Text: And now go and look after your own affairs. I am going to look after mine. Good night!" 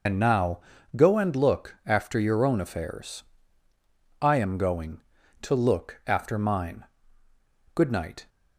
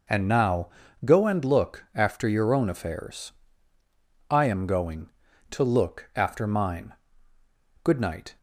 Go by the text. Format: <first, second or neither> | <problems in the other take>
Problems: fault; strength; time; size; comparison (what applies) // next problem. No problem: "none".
second | loses the start of "And"; at 0.0 s; 50 ms // pauses between "now" and "go"; slight; at 0.6 s; 0.34 s long; slight in the second